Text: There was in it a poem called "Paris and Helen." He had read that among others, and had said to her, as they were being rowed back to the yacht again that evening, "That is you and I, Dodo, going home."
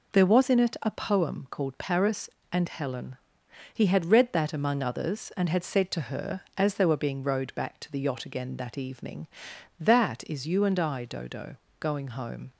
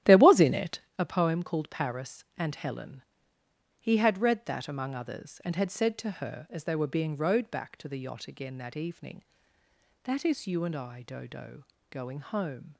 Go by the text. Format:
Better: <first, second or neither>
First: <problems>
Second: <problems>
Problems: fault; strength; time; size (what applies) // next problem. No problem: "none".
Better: first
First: none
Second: starts louder than the rest; strong; until 0.9 s; 12.5 dB // pauses between "it" and "a"; slight; at 0.7 s; 0.18 s long